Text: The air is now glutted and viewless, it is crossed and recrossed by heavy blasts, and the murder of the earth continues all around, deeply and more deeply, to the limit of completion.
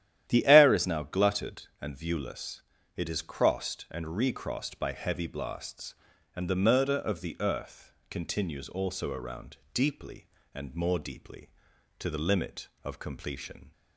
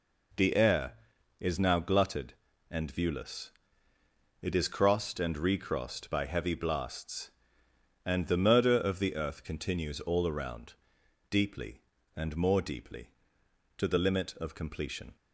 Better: second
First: starts louder than the rest; strong; until 1.2 s; 11.5 dB // pauses between "earth" and "continues"; slight; at 7.9 s; 0.18 s long // says "also" for "all"; at 8.6 s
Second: none

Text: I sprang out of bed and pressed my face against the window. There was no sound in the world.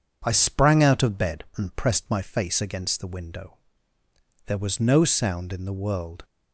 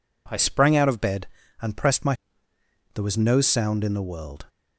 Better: first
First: none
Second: skips "face against the window"; at 2.5 s

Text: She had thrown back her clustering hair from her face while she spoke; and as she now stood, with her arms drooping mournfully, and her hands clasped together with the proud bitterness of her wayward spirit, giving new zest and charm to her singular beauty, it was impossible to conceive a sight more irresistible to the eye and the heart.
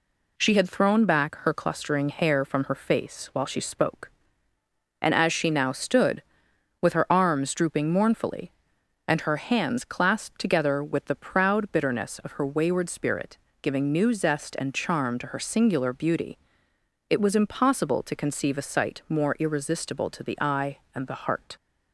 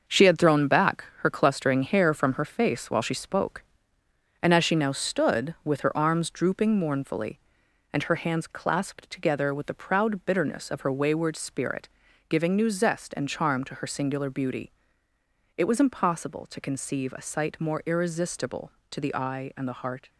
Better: first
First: none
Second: gets quieter; strong; throughout; 7.5 dB

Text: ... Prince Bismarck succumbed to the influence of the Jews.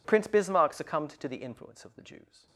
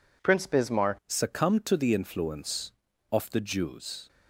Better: first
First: none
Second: changes voice at "succumbed"; from 1.0 s on; 3.0 s long

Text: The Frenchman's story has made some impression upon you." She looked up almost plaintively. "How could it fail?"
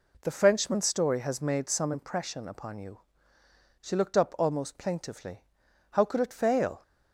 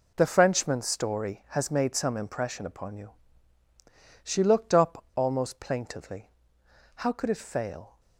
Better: first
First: none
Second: gets quieter; strong; throughout; 11 dB

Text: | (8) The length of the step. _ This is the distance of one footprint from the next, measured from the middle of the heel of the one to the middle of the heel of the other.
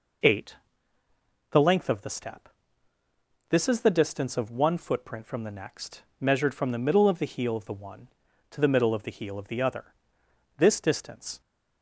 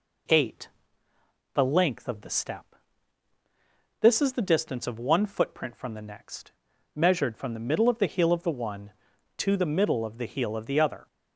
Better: second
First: goes on to say "This distance"; noticeable; from 10.5 s on; 0.82 s long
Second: none

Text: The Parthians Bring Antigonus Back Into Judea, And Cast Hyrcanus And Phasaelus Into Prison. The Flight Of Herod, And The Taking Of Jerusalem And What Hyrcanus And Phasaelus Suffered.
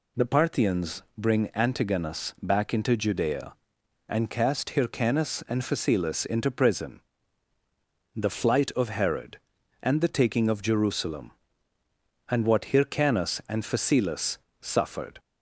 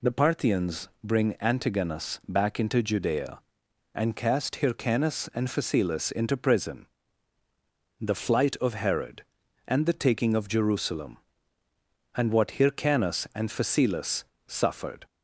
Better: neither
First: pauses between "Phasaelus" and "Suffered"; slight; at 14.3 s; 0.22 s long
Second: pauses between "Phasaelus" and "Suffered"; slight; at 14.2 s; 0.22 s long

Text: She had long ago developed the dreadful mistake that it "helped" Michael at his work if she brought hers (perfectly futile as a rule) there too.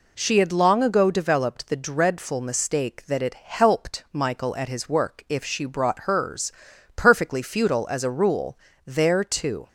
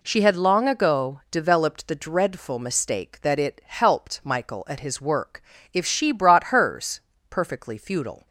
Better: first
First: none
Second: pauses between "work" and "if"; slight; at 5.4 s; 0.32 s long // stops before "as a rule there too"; at 8.2 s

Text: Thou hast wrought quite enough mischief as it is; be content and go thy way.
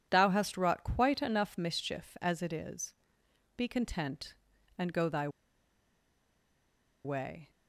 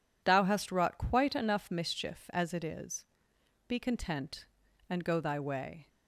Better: second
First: pauses between "thy" and "way"; strong; at 5.2 s; 1.7 s long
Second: none

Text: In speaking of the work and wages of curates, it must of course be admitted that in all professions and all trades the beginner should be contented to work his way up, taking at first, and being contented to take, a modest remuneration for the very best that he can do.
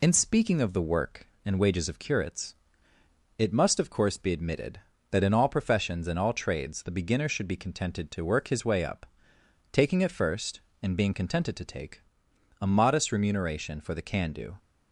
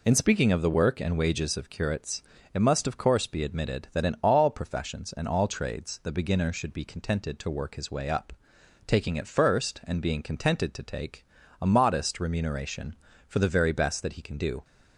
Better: second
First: skips "very best that he"; at 14.0 s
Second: none

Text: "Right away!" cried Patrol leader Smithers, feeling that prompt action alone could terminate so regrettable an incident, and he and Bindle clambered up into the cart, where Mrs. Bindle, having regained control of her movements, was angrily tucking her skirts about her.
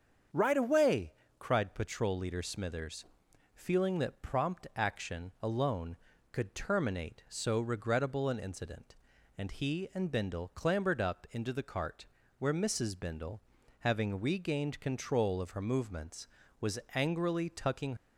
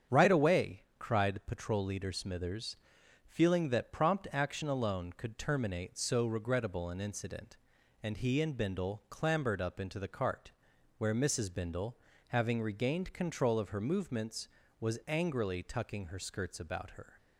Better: second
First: starts louder than the rest; strong; until 1.5 s; 7 dB // pauses between "was" and "angrily"; slight; at 16.7 s; 0.16 s long // stops before "her skirts about her"; at 17.9 s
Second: starts louder than the rest; strong; until 1.2 s; 8 dB

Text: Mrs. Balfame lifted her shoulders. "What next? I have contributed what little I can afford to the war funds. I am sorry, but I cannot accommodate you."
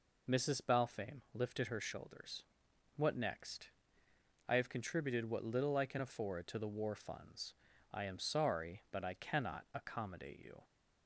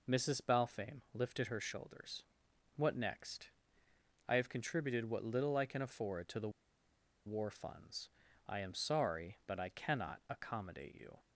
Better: first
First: none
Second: pauses between "the" and "war"; noticeable; at 6.4 s; 0.76 s long

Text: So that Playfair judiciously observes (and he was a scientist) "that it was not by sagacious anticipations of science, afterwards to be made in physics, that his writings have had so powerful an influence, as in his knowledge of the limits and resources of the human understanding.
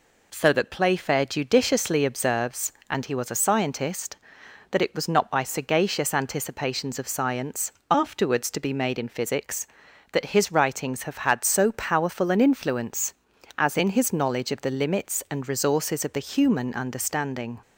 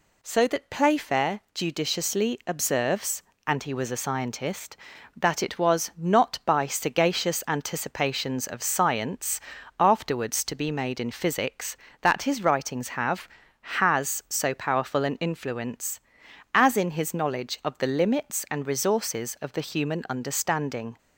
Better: first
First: none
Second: says "has" for "had"; at 13.6 s

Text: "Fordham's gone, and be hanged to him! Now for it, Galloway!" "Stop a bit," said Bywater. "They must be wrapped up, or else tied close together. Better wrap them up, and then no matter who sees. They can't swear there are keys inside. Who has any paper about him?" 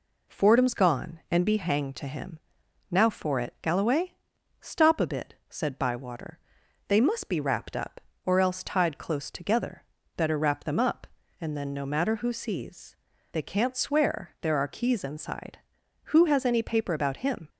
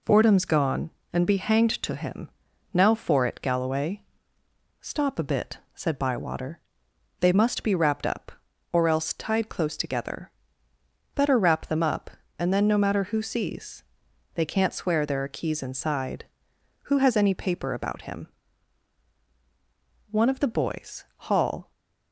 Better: first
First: none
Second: goes on to say "One of the boys Hall"; from 20.1 s on; 1.6 s long

